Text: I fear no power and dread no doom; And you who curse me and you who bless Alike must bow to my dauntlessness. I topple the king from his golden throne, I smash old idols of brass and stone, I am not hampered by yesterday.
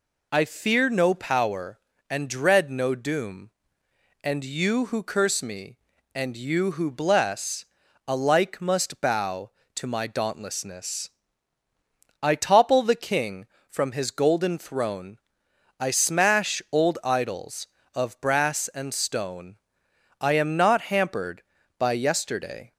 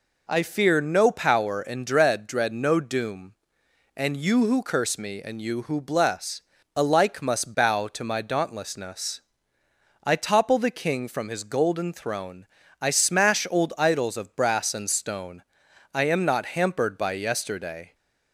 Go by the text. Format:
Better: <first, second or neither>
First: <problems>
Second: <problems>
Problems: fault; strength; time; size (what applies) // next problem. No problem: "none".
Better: first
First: pauses between "bless" and "Alike"; at 7.6 s; 0.42 s long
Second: says "dread" twice; at 2.2 s // pauses between "bless" and "Alike"; slight; at 6.4 s; 0.34 s long